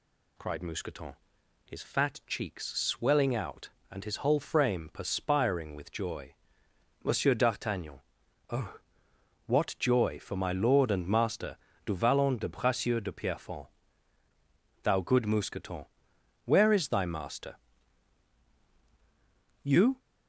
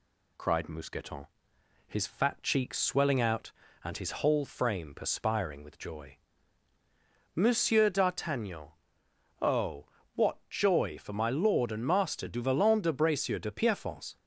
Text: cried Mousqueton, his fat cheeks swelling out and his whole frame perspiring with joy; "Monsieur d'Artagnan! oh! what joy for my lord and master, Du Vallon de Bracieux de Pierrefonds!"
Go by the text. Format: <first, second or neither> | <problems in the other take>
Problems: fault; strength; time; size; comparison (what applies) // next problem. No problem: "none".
second | goes on to say "Thou good Mousqueton where is thy master You"; strong; from 14.8 s on; 5.1 s long